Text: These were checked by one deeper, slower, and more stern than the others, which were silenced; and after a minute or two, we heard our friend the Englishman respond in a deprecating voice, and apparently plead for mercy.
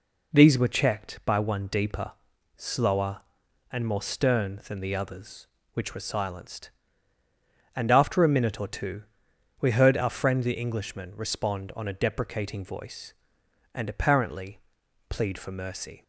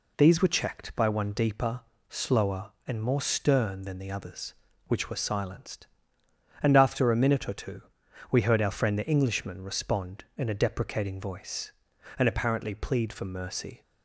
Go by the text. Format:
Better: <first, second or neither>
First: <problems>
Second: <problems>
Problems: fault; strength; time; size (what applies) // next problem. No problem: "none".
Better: second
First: says "on" for "in"; at 11.7 s // pauses between "apparently" and "plead"; noticeable; at 14.5 s; 0.50 s long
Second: none